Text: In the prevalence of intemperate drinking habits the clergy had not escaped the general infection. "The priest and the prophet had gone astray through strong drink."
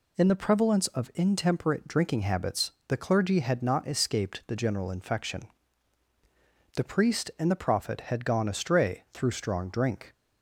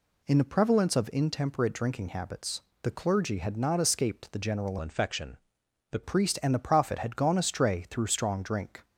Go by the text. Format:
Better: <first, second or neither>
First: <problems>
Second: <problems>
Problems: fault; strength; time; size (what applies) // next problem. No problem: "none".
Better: first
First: pauses between "habits" and "the"; slight; at 2.6 s; 0.16 s long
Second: pauses between "habits" and "the"; slight; at 2.6 s; 0.22 s long // changes voice from "infection" to "The"; from 4.8 to 6.0 s; 1.2 s long